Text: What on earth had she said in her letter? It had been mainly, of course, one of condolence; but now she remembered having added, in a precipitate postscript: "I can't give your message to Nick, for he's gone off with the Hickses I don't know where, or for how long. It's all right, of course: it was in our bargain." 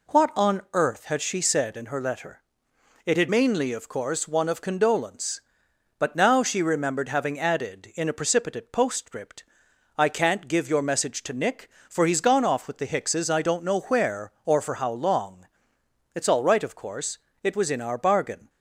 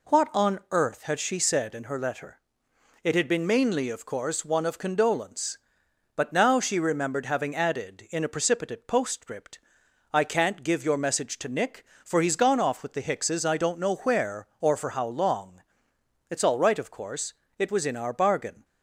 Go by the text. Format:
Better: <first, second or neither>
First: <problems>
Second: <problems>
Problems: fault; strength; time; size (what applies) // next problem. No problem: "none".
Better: second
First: skips "been"; at 3.2 s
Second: none